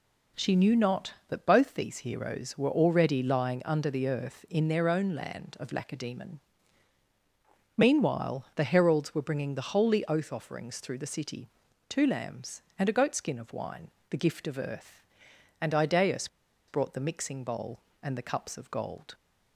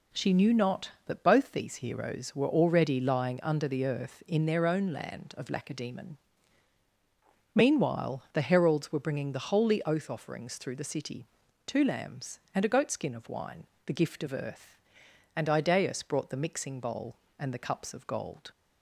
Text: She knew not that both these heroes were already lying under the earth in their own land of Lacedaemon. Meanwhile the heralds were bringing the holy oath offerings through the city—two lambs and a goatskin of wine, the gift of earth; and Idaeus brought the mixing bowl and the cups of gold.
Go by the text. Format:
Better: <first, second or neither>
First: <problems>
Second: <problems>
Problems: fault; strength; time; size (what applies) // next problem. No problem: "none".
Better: second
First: pauses between "Idaeus" and "brought"; at 16.2 s; 0.41 s long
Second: none